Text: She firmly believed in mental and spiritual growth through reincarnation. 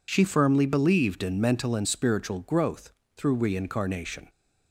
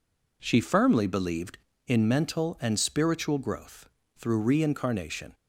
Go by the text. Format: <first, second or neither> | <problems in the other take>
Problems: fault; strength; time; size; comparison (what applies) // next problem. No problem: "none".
neither | pauses between "growth" and "through"; slight; the same in both